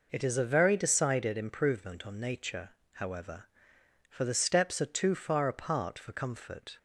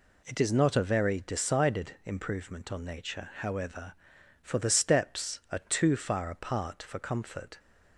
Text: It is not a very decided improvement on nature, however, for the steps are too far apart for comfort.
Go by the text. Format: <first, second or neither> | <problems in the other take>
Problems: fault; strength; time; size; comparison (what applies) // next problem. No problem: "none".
second | skips "not"; at 0.3 s